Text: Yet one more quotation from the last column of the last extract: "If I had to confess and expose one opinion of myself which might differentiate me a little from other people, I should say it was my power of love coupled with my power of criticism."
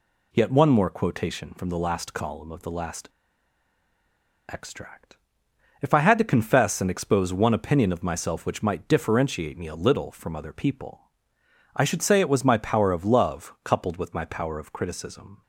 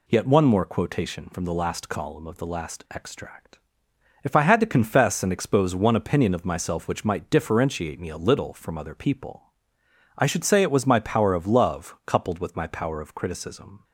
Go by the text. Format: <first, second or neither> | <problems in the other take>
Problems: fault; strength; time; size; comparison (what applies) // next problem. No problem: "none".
second | pauses between "last" and "extract"; strong; at 3.0 s; 1.3 s long